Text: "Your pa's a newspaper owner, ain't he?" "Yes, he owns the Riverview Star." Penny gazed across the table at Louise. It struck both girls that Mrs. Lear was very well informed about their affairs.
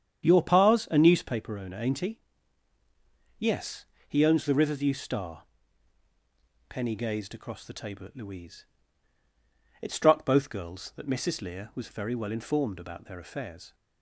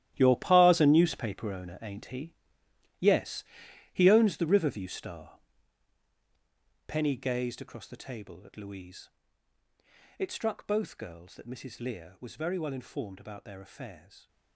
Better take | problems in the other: first | gets quieter; strong; throughout; 12.5 dB // starts louder than the rest; strong; until 1.1 s; 12.5 dB; strong in the first

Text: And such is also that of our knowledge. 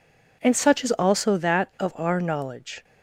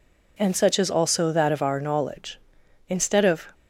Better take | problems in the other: first | goes on to say "Instead of"; noticeable; from 2.8 s on; 0.66 s long

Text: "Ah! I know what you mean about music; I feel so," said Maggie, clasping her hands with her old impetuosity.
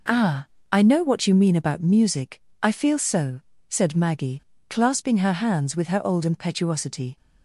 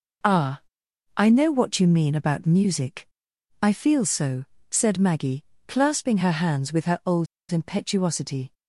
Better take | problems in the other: first | pauses between "old" and "impetuosity"; slight; at 7.2 s; 0.25 s long

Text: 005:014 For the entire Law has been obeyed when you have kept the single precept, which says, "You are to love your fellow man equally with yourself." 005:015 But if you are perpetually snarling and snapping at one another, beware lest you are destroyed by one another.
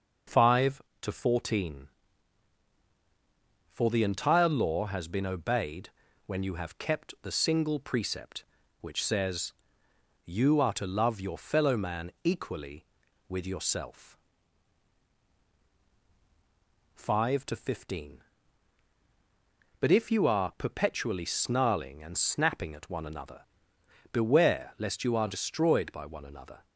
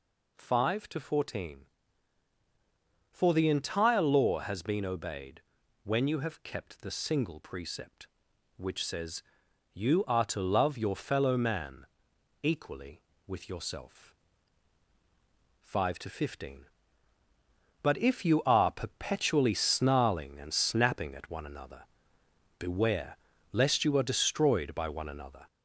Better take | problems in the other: first | gets louder; slight; throughout; 2.5 dB // pauses between "obeyed" and "when"; at 5.4 s; 0.44 s long; also in the first // pauses between "man" and "equally"; noticeable; at 11.8 s; 0.56 s long // pauses between "beware" and "lest"; slight; at 23.1 s; 0.36 s long

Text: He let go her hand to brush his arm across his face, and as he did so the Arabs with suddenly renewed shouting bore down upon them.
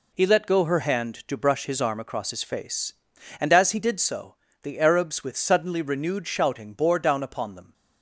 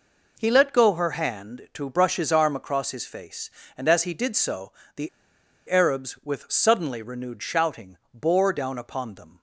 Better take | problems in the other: first | pauses between "so" and "the"; slight; at 4.7 s; 0.24 s long; slight in the first // pauses between "the" and "Arabs"; noticeable; at 5.0 s; 0.59 s long // pauses between "shouting" and "bore"; slight; at 7.9 s; 0.16 s long

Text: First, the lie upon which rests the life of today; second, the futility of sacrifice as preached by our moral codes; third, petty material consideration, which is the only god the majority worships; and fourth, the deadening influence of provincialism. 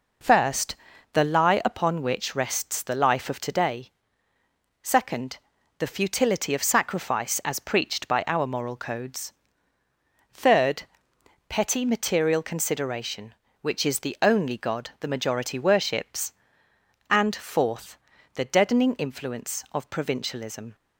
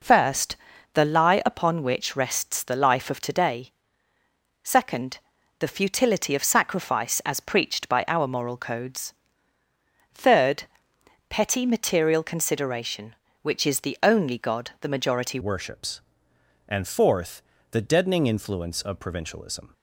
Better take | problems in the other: first | changes voice at "worships"; from 15.4 s on; 4.3 s long

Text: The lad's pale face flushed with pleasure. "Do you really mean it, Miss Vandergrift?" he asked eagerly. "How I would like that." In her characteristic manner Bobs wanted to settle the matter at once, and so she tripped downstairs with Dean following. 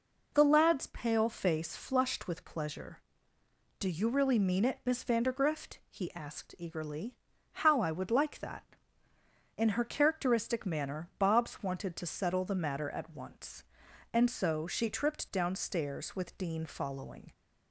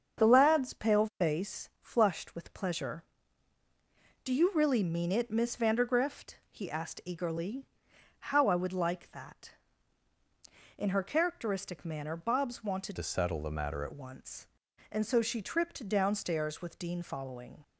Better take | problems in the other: first | starts louder than the rest; strong; until 1.2 s; 7 dB // changes voice from "to" to "at"; from 12.9 to 13.9 s; 1.0 s long

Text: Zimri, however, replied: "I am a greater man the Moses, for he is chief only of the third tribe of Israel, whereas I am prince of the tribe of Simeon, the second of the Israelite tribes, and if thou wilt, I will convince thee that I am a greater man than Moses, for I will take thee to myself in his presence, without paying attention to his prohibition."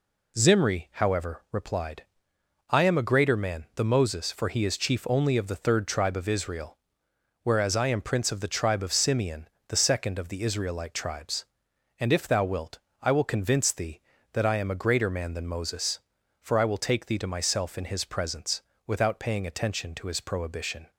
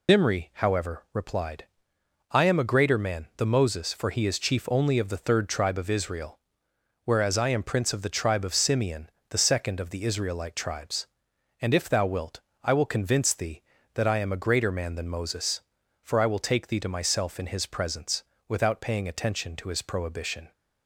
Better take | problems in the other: first | loses the start of "Zimri"; at 0.0 s; 120 ms

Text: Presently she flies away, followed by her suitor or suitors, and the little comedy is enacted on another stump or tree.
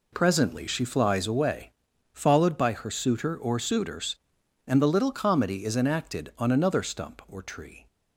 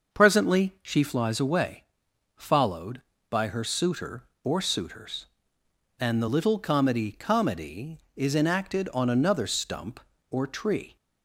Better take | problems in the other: first | starts louder than the rest; until 1.2 s; 6 dB // says "comedy" twice; at 7.1 s

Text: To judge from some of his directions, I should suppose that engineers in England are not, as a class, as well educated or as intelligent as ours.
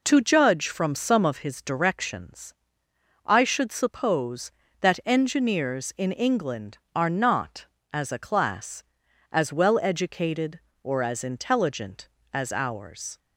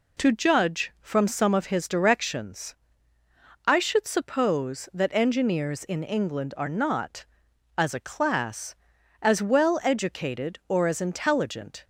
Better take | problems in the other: first | stops before "as ours"; at 11.8 s

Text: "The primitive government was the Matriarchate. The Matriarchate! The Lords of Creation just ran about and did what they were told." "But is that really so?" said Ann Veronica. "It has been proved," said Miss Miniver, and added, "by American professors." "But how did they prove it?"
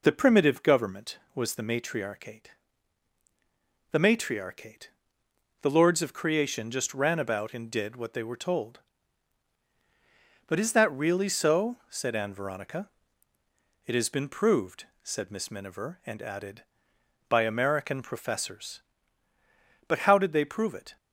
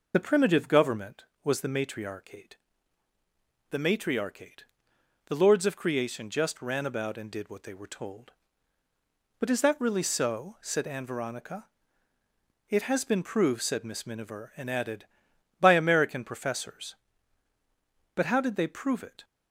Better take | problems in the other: first | loses the start of "The"; at 0.1 s; 35 ms

